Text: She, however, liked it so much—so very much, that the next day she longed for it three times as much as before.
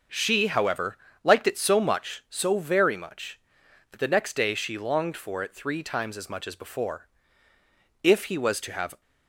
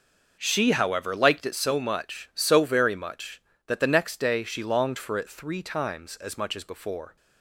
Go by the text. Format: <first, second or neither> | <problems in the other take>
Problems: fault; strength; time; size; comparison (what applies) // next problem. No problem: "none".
second | starts louder than the rest; noticeable; until 1.3 s; 6 dB // goes on to say "If he was to have"; noticeable; from 8.0 s on; 0.98 s long